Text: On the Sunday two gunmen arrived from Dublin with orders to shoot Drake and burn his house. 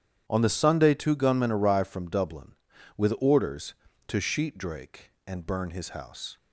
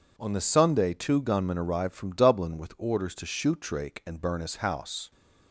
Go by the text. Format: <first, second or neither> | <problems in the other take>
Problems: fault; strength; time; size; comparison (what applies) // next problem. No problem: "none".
second | starts louder than the rest; strong; until 1.2 s; 10 dB // says "sheet" for "shoot"; at 4.2 s